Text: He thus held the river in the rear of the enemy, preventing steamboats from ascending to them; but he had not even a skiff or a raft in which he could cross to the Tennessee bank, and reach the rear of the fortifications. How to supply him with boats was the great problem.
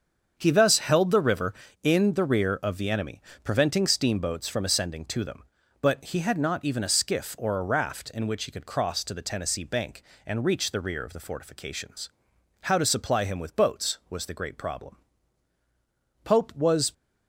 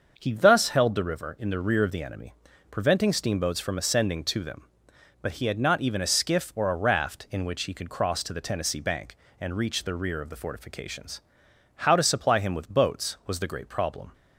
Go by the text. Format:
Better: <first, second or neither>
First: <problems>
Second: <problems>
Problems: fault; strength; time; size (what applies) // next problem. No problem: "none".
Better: second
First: starts louder than the rest; strong; until 1.3 s; 7 dB // goes on to say "Pope was"; noticeable; from 16.2 s on; 0.70 s long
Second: starts louder than the rest; until 1.1 s; 6.5 dB